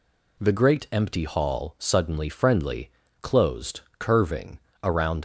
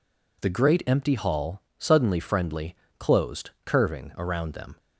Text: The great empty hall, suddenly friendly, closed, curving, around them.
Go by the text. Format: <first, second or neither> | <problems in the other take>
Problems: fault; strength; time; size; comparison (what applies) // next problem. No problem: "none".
second | stops before "them"; at 5.1 s